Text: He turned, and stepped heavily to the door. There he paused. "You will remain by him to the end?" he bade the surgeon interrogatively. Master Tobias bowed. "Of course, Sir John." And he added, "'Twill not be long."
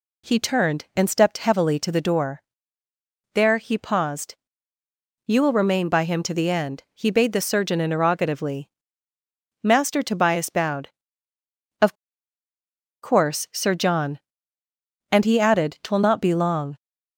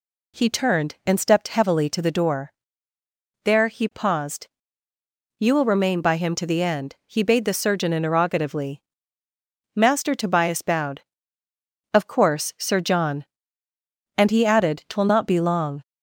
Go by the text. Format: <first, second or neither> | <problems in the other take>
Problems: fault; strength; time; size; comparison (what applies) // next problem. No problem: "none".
second | pauses between "Of" and "course"; at 11.9 s; 1.0 s long